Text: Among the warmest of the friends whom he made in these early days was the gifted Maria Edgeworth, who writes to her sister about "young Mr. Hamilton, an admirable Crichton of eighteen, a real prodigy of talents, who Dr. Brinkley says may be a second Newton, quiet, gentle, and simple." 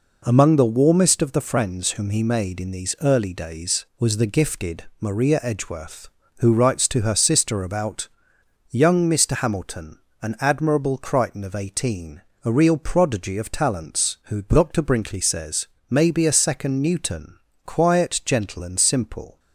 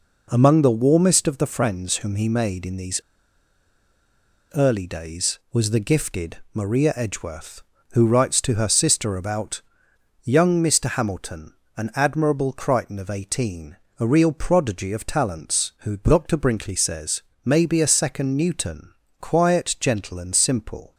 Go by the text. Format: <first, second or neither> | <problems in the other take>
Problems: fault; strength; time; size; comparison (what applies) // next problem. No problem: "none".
first | pauses between "these" and "early"; strong; at 3.0 s; 1.5 s long // pauses between "gifted" and "Maria"; slight; at 6.3 s; 0.16 s long; slight in the first // pauses between "about" and "young"; noticeable; at 9.6 s; 0.64 s long; noticeable in the first // pauses between "says" and "may"; slight; at 17.2 s; 0.24 s long; slight in the first